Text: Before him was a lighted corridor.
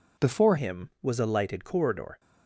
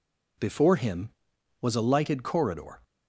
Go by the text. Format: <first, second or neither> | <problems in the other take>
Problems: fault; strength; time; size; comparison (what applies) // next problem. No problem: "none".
second | changes voice at "him"; from 0.5 s on; 1.6 s long